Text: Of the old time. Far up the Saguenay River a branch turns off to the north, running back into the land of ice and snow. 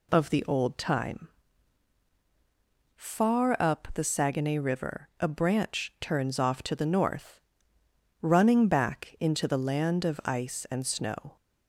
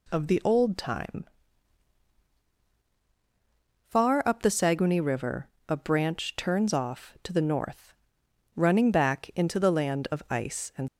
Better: first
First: none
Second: pauses between "River" and "a"; slight; at 5.4 s; 0.20 s long // stops before "snow"; at 10.8 s

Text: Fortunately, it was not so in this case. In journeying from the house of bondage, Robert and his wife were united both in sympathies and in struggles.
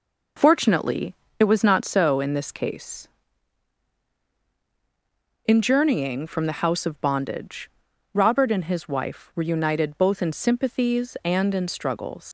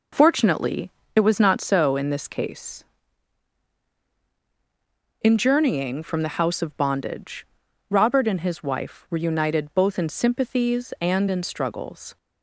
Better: second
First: leaves "struggles" unfinished; at 12.2 s; 100 ms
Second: none

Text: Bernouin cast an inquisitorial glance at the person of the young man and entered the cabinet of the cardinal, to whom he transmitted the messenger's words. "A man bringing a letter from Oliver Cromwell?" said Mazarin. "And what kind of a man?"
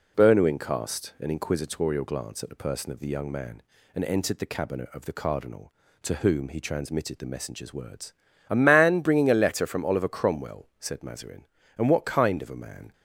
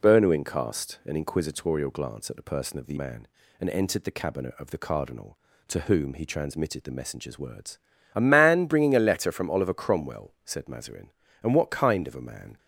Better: first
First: none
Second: skips "young"; at 2.9 s

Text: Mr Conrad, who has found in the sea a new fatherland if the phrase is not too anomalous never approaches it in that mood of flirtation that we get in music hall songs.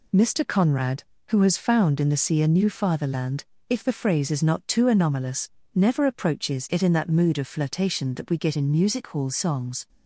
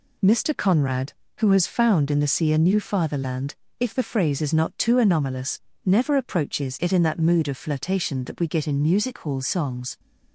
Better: neither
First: pauses between "fatherland" and "if"; slight; at 3.4 s; 0.24 s long // pauses between "anomalous" and "never"; slight; at 5.4 s; 0.26 s long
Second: pauses between "fatherland" and "if"; slight; at 3.5 s; 0.24 s long // pauses between "anomalous" and "never"; slight; at 5.5 s; 0.26 s long

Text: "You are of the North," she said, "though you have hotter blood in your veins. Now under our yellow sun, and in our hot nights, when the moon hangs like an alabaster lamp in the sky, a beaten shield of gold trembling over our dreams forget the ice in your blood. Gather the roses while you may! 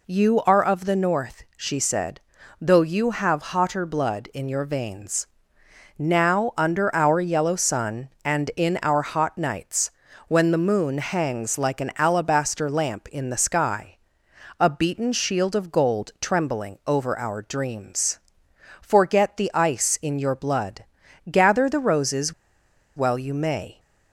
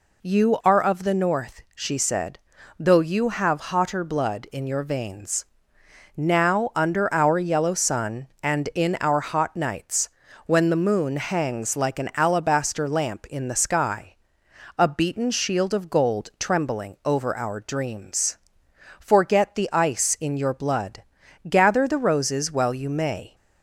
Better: second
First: pauses between "dreams" and "forget"; noticeable; at 18.1 s; 0.62 s long // pauses between "roses" and "while"; noticeable; at 22.3 s; 0.63 s long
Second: pauses between "dreams" and "forget"; noticeable; at 18.3 s; 0.62 s long

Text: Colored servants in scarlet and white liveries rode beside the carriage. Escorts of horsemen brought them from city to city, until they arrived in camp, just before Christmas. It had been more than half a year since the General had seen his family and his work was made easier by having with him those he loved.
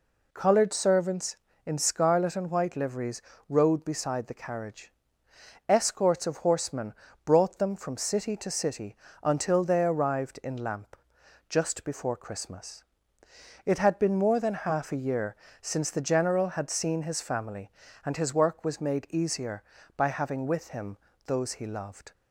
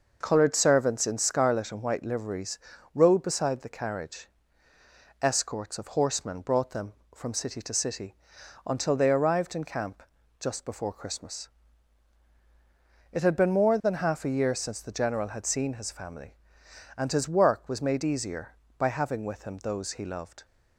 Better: second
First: pauses between "liveries" and "rode"; slight; at 3.2 s; 0.28 s long // pauses between "horsemen" and "brought"; slight; at 6.9 s; 0.32 s long // says "lamp" for "camp"; at 10.5 s // pauses between "year" and "since"; slight; at 15.3 s; 0.24 s long // pauses between "him" and "those"; slight; at 20.9 s; 0.28 s long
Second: pauses between "liveries" and "rode"; slight; at 2.5 s; 0.34 s long

